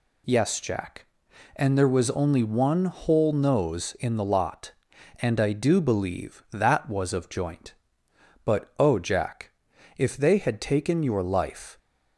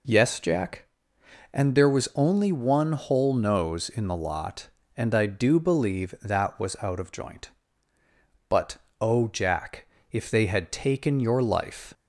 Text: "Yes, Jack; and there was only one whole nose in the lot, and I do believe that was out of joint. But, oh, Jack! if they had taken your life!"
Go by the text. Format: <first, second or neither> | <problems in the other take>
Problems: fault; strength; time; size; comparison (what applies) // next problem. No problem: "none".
second | skips "out"; at 7.1 s